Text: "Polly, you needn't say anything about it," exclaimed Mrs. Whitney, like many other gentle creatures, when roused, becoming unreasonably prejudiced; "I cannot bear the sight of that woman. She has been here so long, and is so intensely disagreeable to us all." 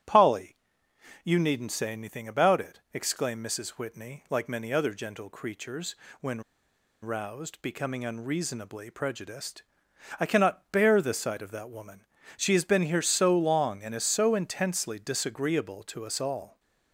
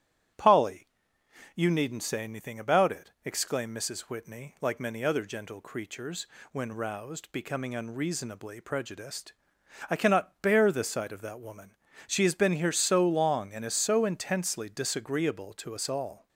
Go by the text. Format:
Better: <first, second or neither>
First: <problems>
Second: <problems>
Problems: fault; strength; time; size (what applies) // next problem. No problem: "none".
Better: second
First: starts louder than the rest; strong; until 1.7 s; 11 dB // pauses between "when" and "roused"; noticeable; at 6.4 s; 0.62 s long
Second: starts louder than the rest; strong; until 2.0 s; 11 dB